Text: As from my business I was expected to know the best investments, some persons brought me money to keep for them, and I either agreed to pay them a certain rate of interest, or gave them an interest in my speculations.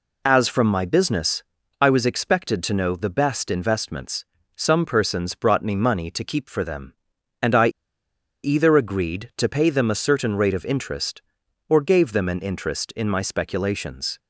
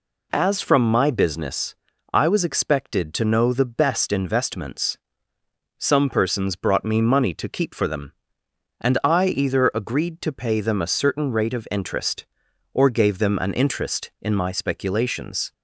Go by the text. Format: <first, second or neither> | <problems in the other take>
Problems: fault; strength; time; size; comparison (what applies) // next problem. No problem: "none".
second | pauses between "business" and "I"; at 1.4 s; 0.38 s long; also in the second // pauses between "I" and "either"; noticeable; at 7.6 s; 0.75 s long